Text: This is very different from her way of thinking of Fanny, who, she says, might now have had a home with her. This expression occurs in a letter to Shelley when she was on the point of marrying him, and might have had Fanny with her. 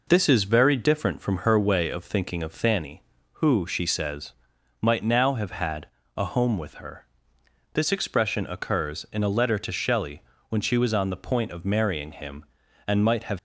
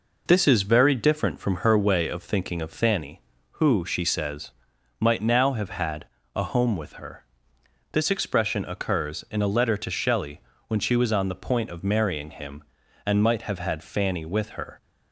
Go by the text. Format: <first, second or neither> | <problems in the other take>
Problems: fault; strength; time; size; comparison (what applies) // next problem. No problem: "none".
second | pauses between "had" and "a"; slight; at 5.8 s; 0.30 s long; slight in the second // pauses between "Shelley" and "when"; slight; at 10.2 s; 0.26 s long; slight in the second // stops before "had Fanny with her"; at 13.3 s